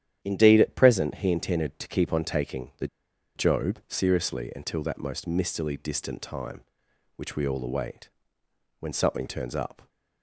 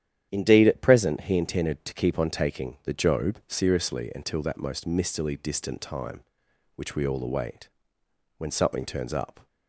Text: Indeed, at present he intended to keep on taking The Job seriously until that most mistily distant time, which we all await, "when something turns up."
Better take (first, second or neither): second